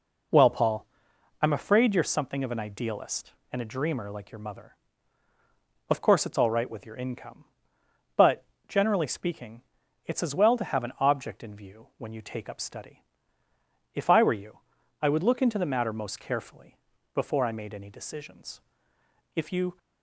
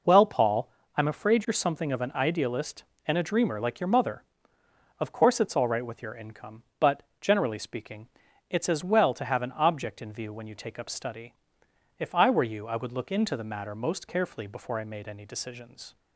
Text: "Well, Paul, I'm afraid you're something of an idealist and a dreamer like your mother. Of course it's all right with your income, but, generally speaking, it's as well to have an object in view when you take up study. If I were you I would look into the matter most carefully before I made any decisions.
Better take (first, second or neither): second